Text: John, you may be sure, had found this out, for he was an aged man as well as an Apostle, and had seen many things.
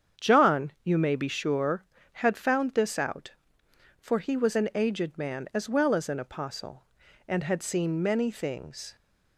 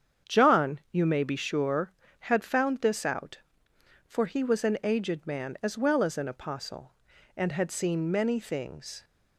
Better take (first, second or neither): neither